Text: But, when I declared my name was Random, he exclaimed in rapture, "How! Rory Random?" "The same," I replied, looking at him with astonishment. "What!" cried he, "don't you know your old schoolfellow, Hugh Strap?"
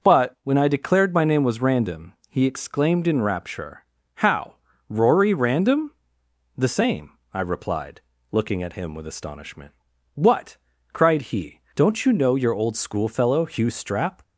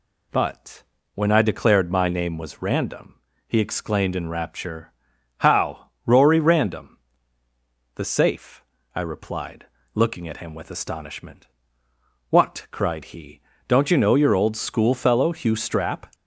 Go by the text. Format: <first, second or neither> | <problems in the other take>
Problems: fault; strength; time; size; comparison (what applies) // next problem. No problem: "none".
first | says "safe" for "same"; at 8.0 s